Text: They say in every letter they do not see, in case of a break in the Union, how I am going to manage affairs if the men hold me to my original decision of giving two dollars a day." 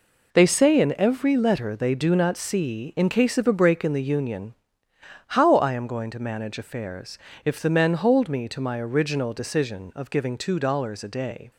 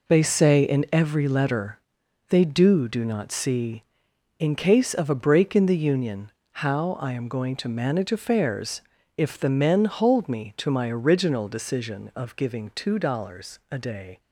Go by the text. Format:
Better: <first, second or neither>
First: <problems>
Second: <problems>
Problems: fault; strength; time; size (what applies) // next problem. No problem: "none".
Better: first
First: pauses between "affairs" and "if"; slight; at 7.1 s; 0.26 s long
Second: pauses between "letter" and "they"; noticeable; at 1.7 s; 0.50 s long // says "do" twice; at 2.8 s // pauses between "affairs" and "if"; slight; at 8.8 s; 0.36 s long